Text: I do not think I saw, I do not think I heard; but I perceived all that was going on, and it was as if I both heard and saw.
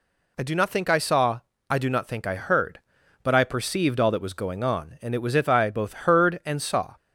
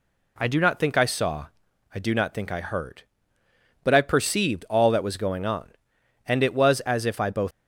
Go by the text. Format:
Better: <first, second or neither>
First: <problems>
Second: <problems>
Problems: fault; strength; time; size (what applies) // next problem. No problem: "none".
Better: first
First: none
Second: stops before "heard and saw"; at 7.5 s